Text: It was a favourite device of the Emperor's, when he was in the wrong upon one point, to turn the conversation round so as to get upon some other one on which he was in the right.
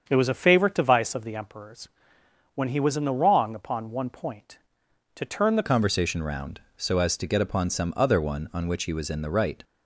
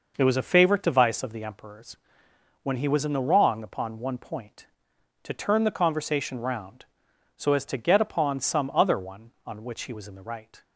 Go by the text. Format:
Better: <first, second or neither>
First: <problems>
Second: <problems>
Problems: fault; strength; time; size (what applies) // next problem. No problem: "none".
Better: second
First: starts louder than the rest; strong; until 1.0 s; 7 dB // changes voice at "conversation"; from 5.6 s on; 4.0 s long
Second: none